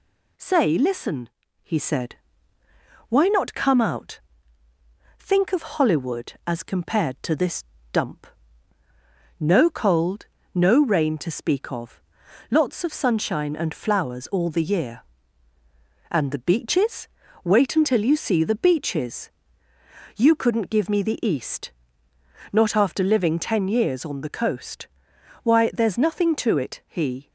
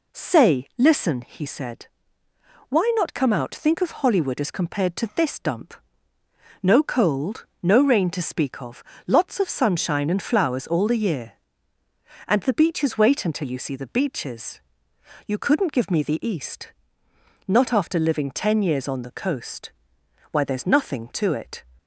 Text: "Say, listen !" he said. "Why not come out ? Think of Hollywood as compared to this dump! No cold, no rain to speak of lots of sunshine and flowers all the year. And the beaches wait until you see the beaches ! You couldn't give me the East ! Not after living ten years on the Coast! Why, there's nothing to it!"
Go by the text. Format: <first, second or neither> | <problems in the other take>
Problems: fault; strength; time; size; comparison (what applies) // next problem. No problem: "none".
second | pauses between "this" and "dump"; slight; at 7.6 s; 0.30 s long // pauses between "of" and "lots"; noticeable; at 12.0 s; 0.48 s long; slight in the second // pauses between "beaches" and "wait"; slight; at 17.0 s; 0.36 s long // goes on to say "He"; slight; from 26.8 s on; 0.44 s long